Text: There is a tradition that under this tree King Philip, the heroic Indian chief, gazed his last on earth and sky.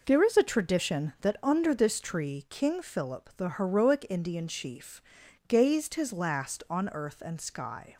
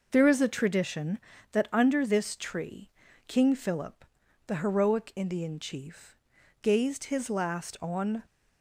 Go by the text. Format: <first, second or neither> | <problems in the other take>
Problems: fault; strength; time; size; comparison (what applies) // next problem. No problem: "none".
first | pauses between "tree" and "King"; at 2.8 s; 0.38 s long // stops before "earth and sky"; at 8.2 s